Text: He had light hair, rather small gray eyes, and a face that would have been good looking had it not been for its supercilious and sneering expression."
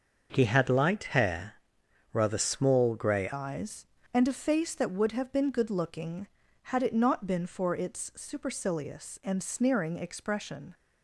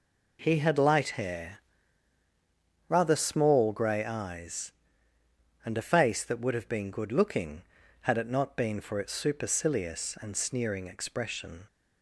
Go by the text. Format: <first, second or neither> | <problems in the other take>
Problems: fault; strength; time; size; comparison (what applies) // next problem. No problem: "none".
second | starts louder than the rest; until 1.4 s; 6 dB // changes voice at "eyes"; from 3.3 s on; 7.4 s long